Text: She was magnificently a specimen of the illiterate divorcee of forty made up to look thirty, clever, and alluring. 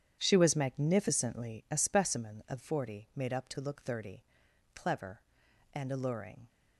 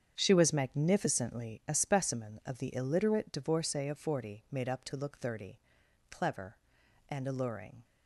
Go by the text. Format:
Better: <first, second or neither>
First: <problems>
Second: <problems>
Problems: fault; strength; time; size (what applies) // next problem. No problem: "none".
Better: second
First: starts louder than the rest; strong; until 1.2 s; 9.5 dB // skips "the illiterate divorcee of"; at 2.6 s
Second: starts louder than the rest; strong; until 1.1 s; 8 dB